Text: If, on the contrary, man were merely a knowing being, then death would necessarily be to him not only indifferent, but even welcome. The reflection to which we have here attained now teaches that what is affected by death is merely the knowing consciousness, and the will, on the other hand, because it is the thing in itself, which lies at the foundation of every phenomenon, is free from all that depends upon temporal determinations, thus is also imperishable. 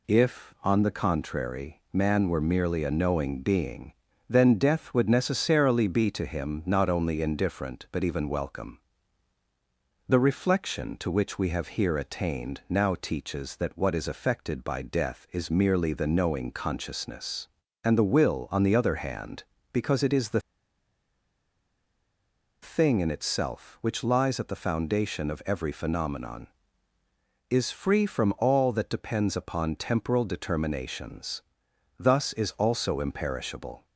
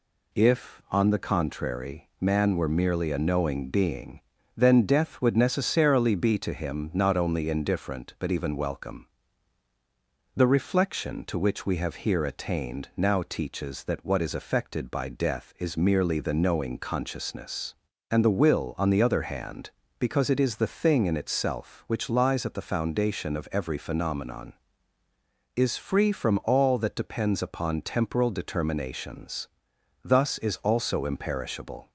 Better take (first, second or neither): second